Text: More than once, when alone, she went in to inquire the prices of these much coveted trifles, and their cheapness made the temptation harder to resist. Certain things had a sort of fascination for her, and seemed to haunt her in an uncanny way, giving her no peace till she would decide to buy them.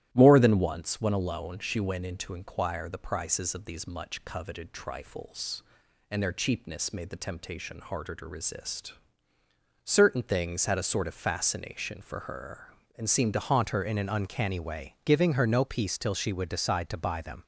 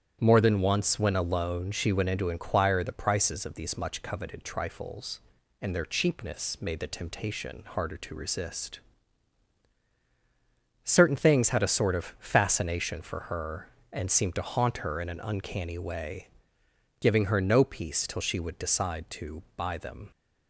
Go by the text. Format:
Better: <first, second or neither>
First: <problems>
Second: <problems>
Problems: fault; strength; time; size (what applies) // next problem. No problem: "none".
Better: second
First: starts louder than the rest; strong; until 1.1 s; 13 dB // changes voice at "haunt"; from 13.4 s on; 4.0 s long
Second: starts louder than the rest; strong; until 1.2 s; 9.5 dB